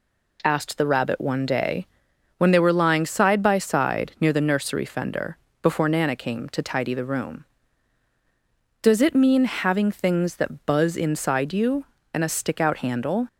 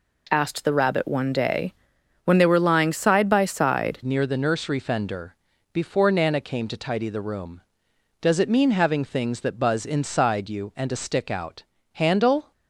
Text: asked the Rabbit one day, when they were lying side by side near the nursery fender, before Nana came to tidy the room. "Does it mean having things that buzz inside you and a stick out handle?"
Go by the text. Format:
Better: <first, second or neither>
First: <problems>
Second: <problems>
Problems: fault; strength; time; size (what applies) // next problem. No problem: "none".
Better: first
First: none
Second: changes voice at "near"; from 4.0 s on; 8.5 s long // pauses between "out" and "handle"; slight; at 11.6 s; 0.30 s long